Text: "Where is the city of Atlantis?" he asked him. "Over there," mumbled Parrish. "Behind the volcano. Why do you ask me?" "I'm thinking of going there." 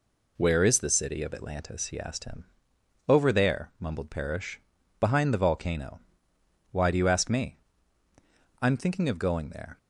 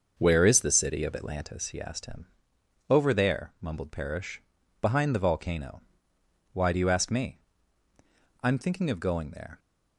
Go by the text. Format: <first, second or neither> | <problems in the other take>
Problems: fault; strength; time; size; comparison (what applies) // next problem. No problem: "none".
first | starts louder than the rest; until 1.6 s; 6.5 dB